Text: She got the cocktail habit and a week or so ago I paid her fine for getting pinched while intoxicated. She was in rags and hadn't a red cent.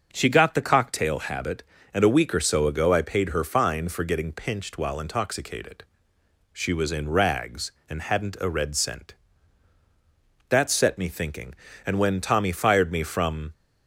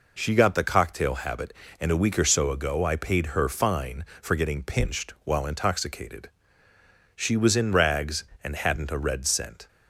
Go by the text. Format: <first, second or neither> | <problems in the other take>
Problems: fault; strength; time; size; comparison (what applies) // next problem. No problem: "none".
second | starts louder than the rest; until 1.1 s; 6 dB // goes on to say "That set me thinking and when Tommy fired me from"; strong; from 10.4 s on; 3.0 s long